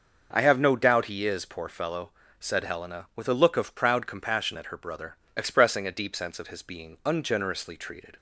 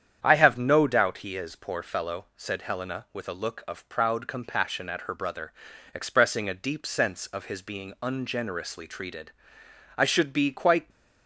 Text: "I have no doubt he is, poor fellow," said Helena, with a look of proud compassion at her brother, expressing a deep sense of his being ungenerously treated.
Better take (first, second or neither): first